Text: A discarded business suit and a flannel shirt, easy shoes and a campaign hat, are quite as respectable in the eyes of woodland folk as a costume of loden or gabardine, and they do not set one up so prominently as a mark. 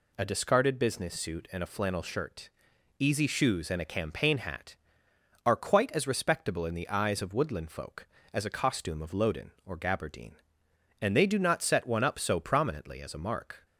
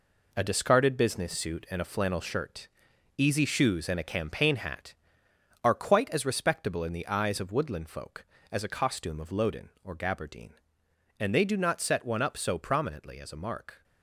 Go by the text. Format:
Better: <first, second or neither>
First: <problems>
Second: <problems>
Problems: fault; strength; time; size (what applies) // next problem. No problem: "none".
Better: first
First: none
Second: gets quieter; strong; throughout; 7.5 dB